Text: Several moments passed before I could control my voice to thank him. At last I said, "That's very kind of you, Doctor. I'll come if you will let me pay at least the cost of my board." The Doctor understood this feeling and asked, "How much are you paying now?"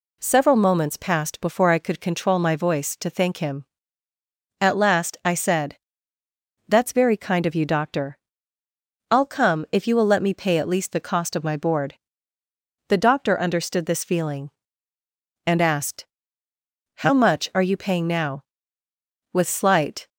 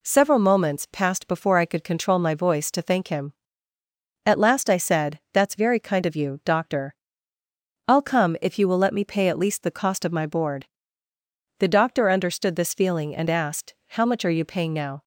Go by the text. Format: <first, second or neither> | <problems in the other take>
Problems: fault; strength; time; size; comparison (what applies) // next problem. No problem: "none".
second | goes on to say "With slight"; noticeable; from 19.3 s on; 0.76 s long